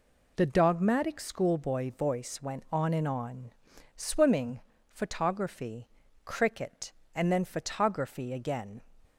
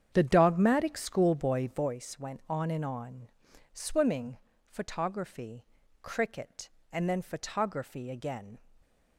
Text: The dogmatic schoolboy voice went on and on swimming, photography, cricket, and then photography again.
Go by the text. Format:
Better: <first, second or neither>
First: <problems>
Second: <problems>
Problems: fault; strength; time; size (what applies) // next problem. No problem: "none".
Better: first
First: pauses between "on" and "swimming"; noticeable; at 3.5 s; 0.46 s long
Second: starts louder than the rest; strong; until 1.9 s; 8.5 dB // pauses between "on" and "swimming"; noticeable; at 3.2 s; 0.46 s long